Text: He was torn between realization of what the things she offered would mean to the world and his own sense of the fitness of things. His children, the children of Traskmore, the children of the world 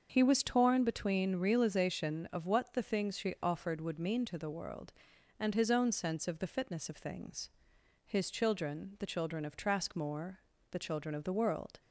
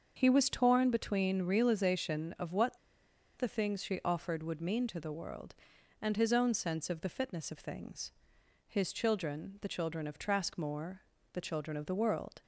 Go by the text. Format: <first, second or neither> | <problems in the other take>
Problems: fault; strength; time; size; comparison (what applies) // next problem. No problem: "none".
first | starts louder than the rest; until 1.1 s; 6.5 dB; also in the first // pauses between "what" and "the"; noticeable; at 2.7 s; 0.59 s long